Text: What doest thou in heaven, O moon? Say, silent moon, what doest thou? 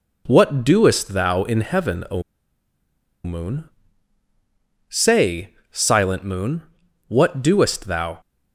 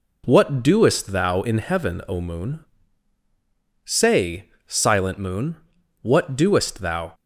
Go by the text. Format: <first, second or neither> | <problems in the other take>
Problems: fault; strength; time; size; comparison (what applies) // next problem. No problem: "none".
second | pauses between "O" and "moon"; at 2.2 s; 1.0 s long